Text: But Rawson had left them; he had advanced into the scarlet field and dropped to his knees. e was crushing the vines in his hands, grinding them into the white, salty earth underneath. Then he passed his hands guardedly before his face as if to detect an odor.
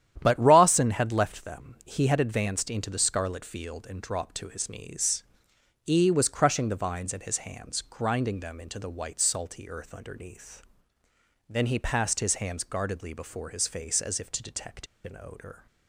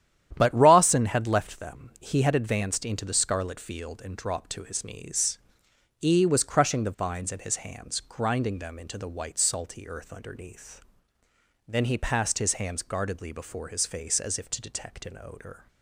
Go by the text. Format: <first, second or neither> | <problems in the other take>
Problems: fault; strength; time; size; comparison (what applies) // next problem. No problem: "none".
second | starts louder than the rest; strong; until 1.2 s; 11 dB; strong in the second // pauses between "detect" and "an"; slight; at 14.8 s; 0.18 s long